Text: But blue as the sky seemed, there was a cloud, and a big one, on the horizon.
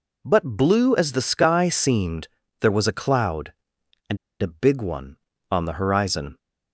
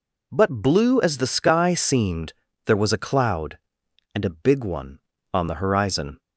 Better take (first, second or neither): second